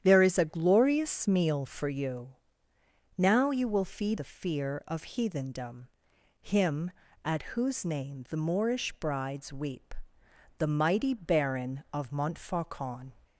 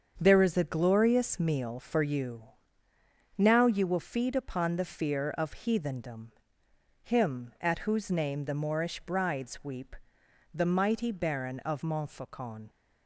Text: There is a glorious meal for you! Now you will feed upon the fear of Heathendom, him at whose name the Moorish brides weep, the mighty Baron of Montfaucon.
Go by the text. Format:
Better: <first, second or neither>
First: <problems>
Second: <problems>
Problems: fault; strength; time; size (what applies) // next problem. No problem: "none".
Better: second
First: starts louder than the rest; strong; until 1.0 s; 10 dB // skips "upon"; at 4.1 s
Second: starts louder than the rest; strong; until 1.1 s; 7 dB